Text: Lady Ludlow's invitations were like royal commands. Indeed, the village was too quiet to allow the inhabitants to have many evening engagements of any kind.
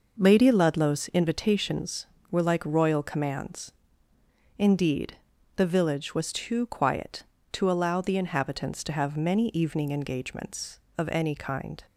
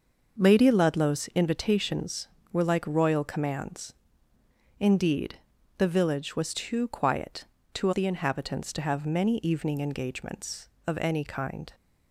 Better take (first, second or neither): first